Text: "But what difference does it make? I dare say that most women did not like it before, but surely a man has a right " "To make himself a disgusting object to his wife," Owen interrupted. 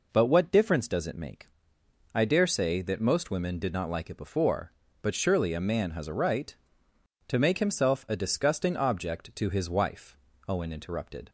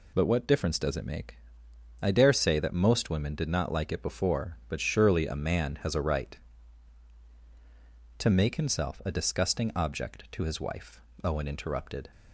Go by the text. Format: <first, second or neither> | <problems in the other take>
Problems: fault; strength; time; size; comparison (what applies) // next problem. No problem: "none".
neither | none